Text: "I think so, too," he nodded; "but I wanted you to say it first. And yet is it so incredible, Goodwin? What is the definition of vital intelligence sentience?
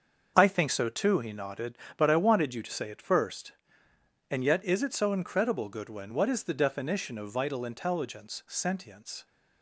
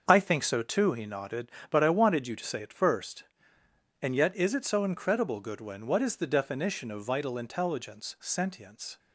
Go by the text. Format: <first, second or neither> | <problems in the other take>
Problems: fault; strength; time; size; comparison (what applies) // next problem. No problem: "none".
neither | starts louder than the rest; the same in both